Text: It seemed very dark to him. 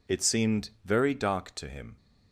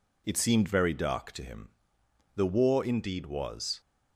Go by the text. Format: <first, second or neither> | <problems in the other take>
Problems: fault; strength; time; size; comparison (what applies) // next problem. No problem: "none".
first | goes on to say "The war indeed was"; from 2.3 s on; 1.4 s long